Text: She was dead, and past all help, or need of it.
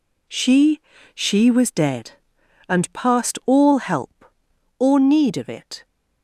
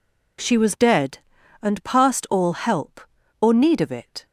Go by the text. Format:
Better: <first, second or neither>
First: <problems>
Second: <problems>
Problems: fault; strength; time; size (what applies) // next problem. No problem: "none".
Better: second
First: says "She" twice; at 1.1 s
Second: none